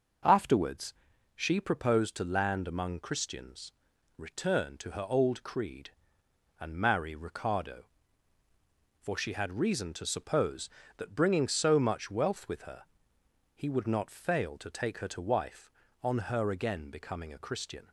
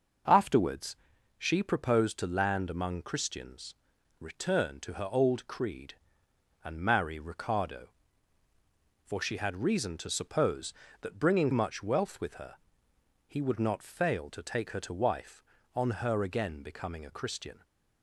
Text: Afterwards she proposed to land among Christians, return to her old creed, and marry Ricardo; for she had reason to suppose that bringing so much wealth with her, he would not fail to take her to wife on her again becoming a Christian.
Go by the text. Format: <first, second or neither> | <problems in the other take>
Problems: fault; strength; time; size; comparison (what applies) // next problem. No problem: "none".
first | starts louder than the rest; noticeable; until 1.6 s; 6 dB; noticeable in the first // pauses between "Afterwards" and "she"; at 0.9 s; 0.42 s long; also in the first // skips "so"; at 11.5 s